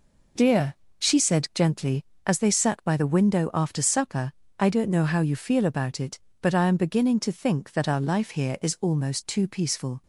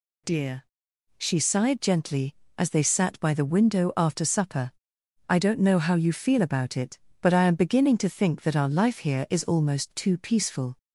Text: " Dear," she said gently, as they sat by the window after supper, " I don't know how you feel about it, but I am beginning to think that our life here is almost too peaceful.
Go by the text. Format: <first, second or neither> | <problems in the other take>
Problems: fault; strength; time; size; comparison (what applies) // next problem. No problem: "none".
first | says "sighed" for "said"; at 1.3 s